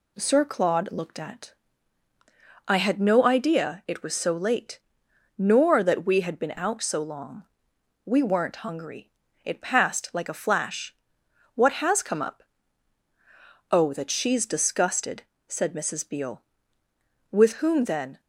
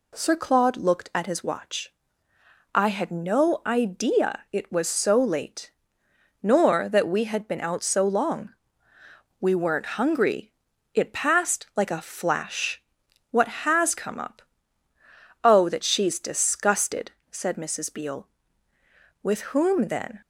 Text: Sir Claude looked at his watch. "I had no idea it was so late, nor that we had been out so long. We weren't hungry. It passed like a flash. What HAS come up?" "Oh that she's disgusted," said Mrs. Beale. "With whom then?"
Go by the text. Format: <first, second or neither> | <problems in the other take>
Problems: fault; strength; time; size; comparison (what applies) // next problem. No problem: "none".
second | skips "his watch"; at 2.1 s